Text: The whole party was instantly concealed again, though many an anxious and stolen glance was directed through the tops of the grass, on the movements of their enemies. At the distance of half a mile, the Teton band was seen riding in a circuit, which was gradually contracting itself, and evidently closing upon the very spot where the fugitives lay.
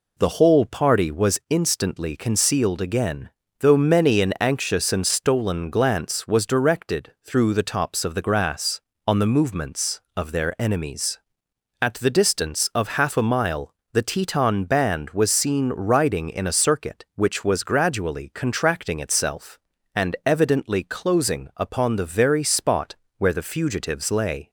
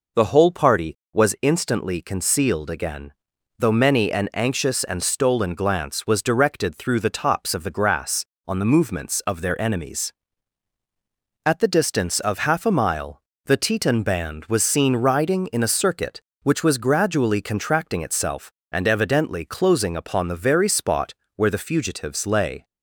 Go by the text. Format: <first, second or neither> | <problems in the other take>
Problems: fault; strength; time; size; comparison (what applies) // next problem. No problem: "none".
first | starts louder than the rest; noticeable; until 1.5 s; 5 dB // pauses between "spot" and "where"; slight; at 21.1 s; 0.22 s long; slight in the first